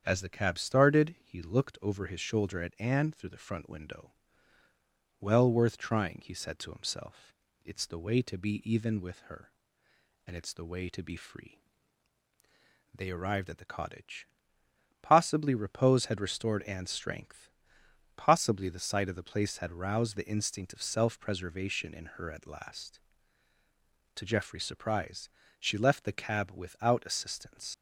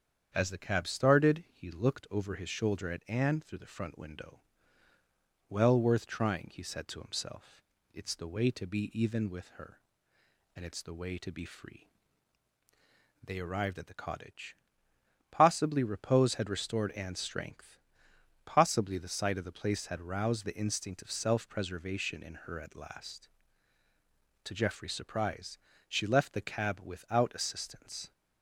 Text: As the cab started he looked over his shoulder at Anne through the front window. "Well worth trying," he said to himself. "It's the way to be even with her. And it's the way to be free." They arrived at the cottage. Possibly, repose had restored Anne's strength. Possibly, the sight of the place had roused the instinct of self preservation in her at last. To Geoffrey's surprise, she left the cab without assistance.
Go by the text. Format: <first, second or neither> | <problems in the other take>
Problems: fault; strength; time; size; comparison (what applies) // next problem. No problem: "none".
second | starts louder than the rest; strong; until 1.0 s; 8 dB; strong in the second // leaves "assistance" unfinished; at 27.7 s; 85 ms